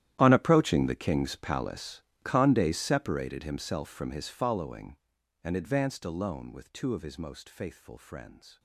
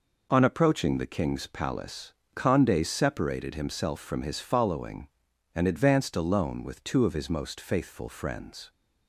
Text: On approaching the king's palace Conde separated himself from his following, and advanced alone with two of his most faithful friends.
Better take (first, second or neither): second